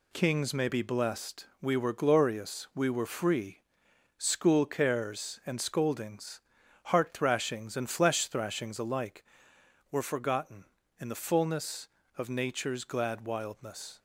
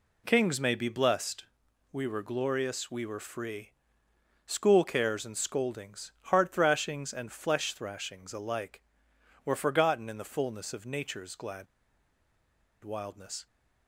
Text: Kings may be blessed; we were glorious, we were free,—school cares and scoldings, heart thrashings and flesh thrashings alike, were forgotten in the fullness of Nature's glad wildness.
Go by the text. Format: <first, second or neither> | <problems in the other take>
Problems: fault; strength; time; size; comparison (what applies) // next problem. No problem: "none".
first | pauses between "glad" and "wildness"; at 11.6 s; 1.1 s long